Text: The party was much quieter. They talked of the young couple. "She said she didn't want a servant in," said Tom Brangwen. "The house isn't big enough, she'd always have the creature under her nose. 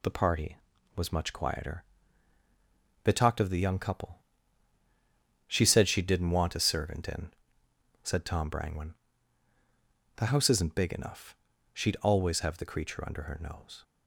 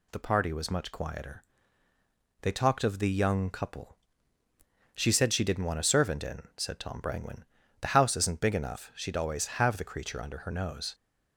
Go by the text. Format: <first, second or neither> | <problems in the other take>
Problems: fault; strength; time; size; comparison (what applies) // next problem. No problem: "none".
neither | none